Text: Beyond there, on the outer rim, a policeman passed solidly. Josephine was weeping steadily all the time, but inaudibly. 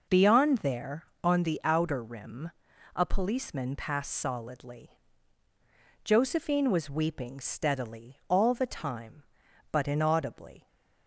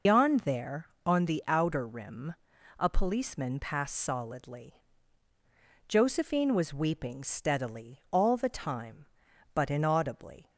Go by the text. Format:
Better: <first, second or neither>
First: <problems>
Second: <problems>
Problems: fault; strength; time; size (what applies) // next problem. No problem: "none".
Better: first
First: none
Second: loses the start of "Beyond"; at 0.0 s; 140 ms